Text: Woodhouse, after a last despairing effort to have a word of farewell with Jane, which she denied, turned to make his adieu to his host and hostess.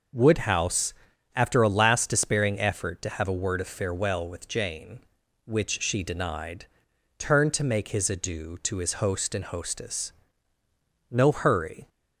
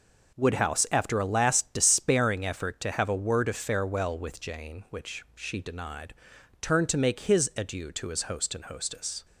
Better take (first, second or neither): second